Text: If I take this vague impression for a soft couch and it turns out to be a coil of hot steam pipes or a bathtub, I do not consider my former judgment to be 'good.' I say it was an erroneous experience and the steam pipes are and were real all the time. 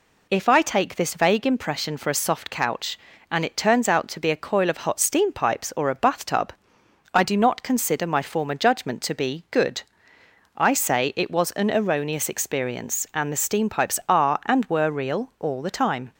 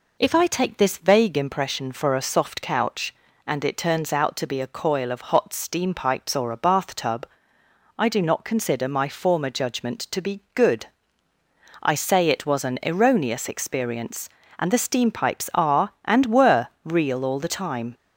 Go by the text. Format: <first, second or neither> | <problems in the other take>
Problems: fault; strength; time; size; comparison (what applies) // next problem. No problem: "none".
neither | none